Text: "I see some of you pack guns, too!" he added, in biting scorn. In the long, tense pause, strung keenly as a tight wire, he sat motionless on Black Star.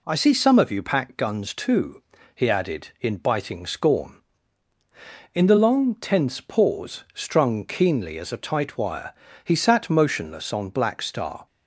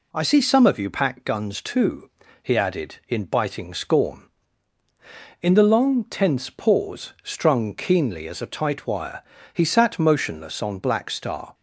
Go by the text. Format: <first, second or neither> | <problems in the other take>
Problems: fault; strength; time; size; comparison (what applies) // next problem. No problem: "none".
neither | none